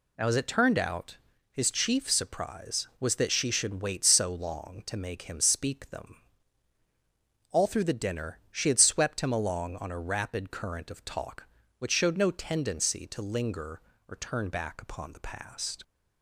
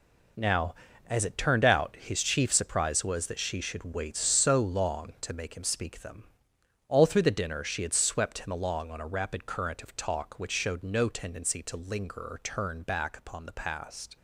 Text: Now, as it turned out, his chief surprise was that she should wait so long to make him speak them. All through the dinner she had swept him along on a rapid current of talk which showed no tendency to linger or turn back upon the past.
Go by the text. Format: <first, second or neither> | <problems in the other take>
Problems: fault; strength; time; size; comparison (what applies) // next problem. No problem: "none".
first | gets quieter; strong; throughout; 10 dB